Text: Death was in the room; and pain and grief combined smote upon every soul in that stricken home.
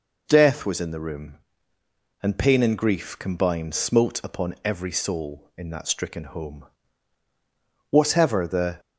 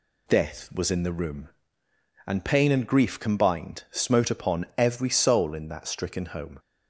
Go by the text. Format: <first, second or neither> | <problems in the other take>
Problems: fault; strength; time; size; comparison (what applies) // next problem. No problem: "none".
second | goes on to say "Whatever the"; noticeable; from 7.8 s on; 0.90 s long